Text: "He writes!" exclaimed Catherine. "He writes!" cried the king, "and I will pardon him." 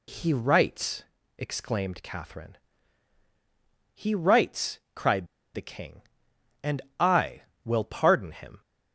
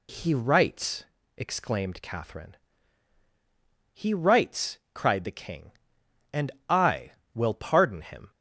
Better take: second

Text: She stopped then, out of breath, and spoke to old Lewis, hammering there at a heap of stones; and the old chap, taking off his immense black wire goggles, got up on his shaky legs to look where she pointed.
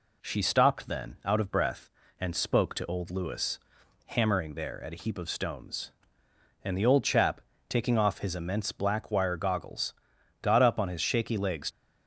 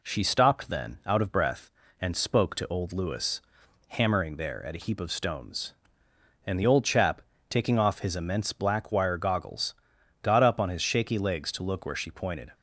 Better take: second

